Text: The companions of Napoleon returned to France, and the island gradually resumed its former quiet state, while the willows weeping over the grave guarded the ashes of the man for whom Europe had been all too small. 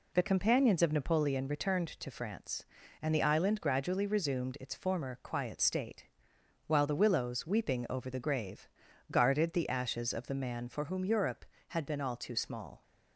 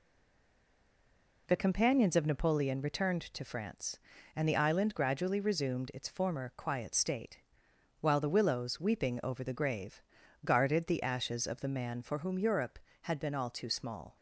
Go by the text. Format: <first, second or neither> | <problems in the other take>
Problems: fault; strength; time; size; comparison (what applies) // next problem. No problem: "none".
first | stays silent before the first word; noticeable; until 1.4 s; 1.4 s long // pauses between "grave" and "guarded"; at 10.0 s; 0.44 s long; also in the first